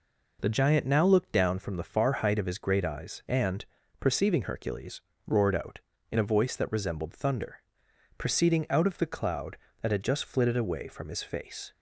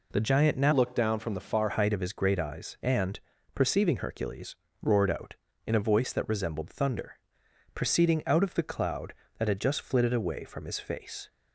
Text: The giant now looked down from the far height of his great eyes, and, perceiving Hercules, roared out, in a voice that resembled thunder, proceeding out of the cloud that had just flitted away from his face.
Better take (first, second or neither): first